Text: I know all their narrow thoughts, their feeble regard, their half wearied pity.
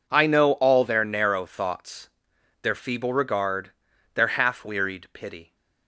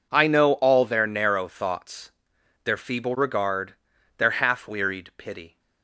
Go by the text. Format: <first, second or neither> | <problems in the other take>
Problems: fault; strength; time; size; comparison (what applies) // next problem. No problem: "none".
neither | none